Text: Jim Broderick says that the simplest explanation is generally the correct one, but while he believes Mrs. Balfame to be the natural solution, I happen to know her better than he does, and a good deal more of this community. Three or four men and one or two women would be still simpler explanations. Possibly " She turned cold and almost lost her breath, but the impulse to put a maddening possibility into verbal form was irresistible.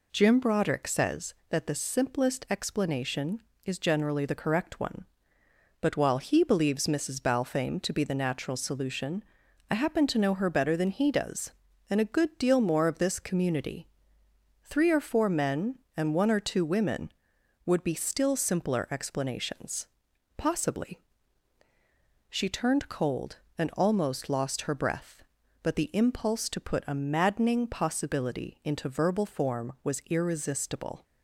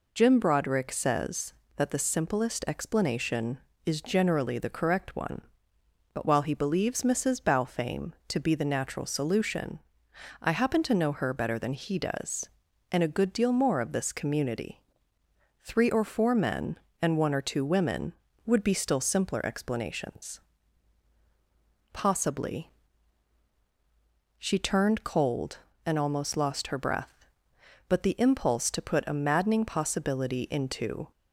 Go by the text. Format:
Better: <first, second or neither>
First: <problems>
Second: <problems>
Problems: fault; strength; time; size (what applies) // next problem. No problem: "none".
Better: first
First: none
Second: stops before "verbal form was irresistible"; at 31.1 s